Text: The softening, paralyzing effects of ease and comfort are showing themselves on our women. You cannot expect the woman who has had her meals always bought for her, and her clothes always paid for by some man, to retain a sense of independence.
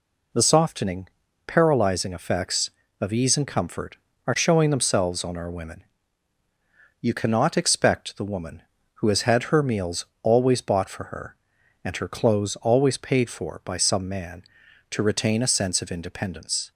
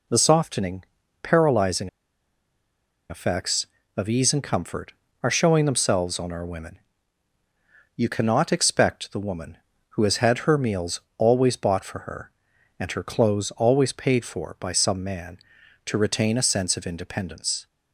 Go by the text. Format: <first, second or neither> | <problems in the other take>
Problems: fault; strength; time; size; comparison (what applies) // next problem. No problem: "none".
first | pauses between "paralyzing" and "effects"; at 1.8 s; 1.2 s long // pauses between "meals" and "always"; slight; at 10.9 s; 0.18 s long; slight in the first